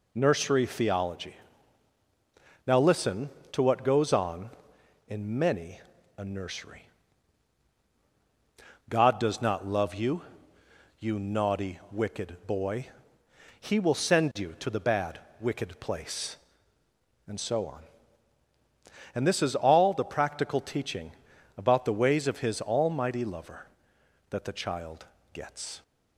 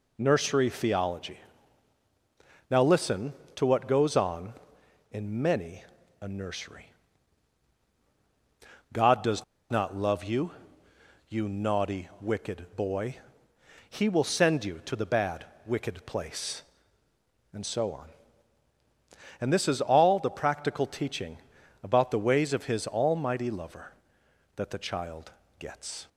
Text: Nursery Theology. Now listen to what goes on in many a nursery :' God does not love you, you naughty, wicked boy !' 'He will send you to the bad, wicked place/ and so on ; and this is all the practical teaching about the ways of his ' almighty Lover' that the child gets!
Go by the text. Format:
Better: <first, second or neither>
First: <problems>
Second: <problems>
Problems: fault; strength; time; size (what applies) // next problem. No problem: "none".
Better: first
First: pauses between "many" and "a"; slight; at 5.8 s; 0.36 s long // pauses between "teaching" and "about"; at 21.1 s; 0.44 s long // pauses between "child" and "gets"; slight; at 25.0 s; 0.26 s long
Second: pauses between "many" and "a"; slight; at 5.8 s; 0.36 s long // pauses between "does" and "not"; slight; at 9.4 s; 0.26 s long // pauses between "teaching" and "about"; at 21.3 s; 0.44 s long // pauses between "child" and "gets"; slight; at 25.3 s; 0.26 s long